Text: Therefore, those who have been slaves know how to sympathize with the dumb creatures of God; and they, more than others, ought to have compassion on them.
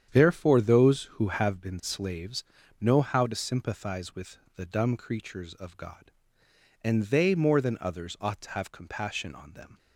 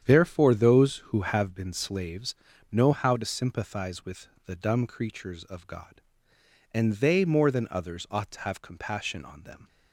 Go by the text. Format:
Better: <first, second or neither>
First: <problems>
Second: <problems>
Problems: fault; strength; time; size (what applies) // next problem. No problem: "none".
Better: neither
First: starts louder than the rest; strong; until 1.1 s; 8.5 dB // pauses between "slaves" and "know"; slight; at 2.4 s; 0.36 s long // pauses between "with" and "the"; slight; at 4.3 s; 0.18 s long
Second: starts louder than the rest; strong; until 1.0 s; 8.5 dB // pauses between "slaves" and "know"; slight; at 2.3 s; 0.36 s long // pauses between "with" and "the"; slight; at 4.2 s; 0.18 s long